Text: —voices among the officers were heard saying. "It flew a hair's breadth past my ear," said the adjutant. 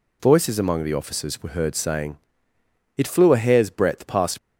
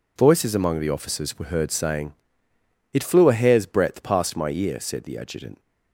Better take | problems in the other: second | stops before "my ear said the adjutant"; at 4.3 s

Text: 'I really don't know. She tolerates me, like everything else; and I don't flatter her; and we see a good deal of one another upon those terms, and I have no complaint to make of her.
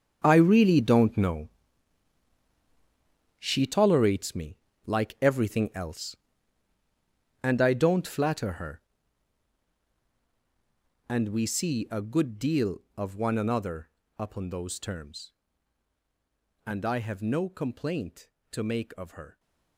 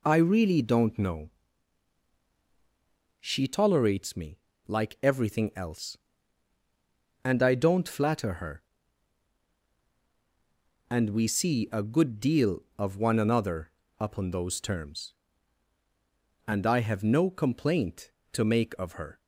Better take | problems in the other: second | gets quieter; strong; throughout; 14 dB // pauses between "another" and "upon"; slight; at 13.8 s; 0.26 s long; slight in the second

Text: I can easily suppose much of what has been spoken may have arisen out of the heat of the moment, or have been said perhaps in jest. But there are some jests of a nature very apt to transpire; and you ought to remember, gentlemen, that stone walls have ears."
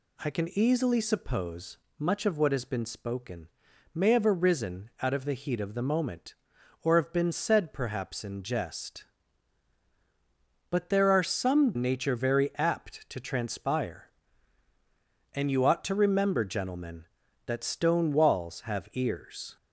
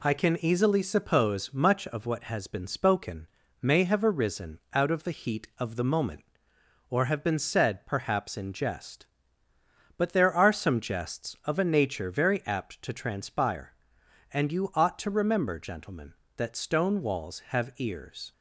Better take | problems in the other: second | pauses between "suppose" and "much"; slight; at 1.7 s; 0.22 s long // pauses between "spoken" and "may"; at 3.4 s; 0.44 s long; slight in the second // skips "jests of a"; at 11.7 s

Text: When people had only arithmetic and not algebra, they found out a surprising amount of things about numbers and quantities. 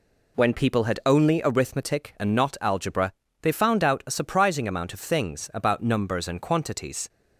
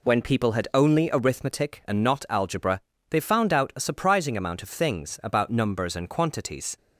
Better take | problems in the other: neither | none

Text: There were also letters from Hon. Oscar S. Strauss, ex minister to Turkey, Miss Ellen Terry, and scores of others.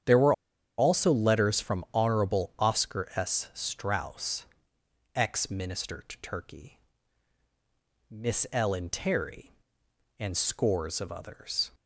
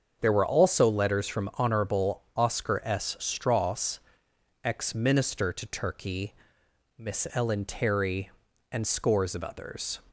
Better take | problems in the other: second | starts louder than the rest; strong; until 1.5 s; 9 dB; also in the second // pauses between "were" and "also"; at 0.3 s; 0.44 s long

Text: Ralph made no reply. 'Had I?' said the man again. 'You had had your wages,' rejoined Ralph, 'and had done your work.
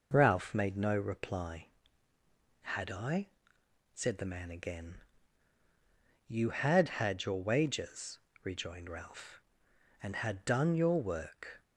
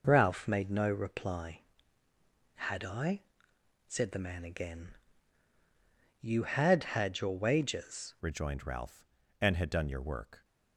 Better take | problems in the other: first | changes voice at "rejoined"; from 8.2 s on; 2.2 s long

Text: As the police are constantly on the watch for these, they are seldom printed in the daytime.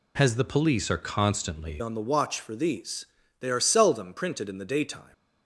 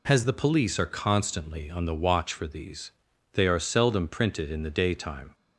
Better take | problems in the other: second | changes voice at "on"; from 1.7 s on; 3.4 s long

